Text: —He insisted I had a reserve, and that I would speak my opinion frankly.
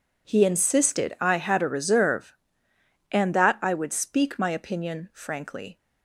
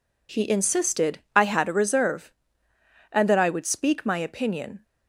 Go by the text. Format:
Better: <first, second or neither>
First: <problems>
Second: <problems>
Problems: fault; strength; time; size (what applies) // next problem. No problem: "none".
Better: first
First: none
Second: pauses between "insisted" and "I"; slight; at 1.1 s; 0.16 s long // stops before "frankly"; at 4.8 s